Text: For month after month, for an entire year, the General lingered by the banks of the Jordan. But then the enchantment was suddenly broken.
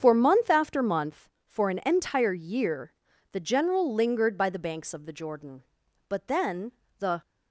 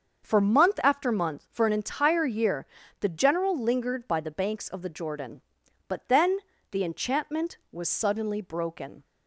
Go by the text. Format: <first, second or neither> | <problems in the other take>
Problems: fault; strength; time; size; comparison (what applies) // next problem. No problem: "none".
second | starts louder than the rest; strong; until 1.0 s; 7.5 dB; also in the second // pauses between "then" and "the"; slight; at 6.7 s; 0.26 s long; slight in the second // stops before "enchantment was suddenly broken"; at 7.2 s